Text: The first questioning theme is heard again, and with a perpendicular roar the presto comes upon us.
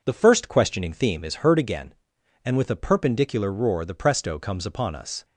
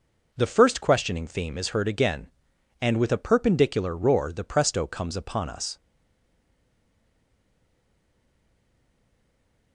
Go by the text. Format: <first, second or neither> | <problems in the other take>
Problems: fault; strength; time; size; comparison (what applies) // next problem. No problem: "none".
first | stays silent after the last word; strong; from 5.7 s on; 4.0 s long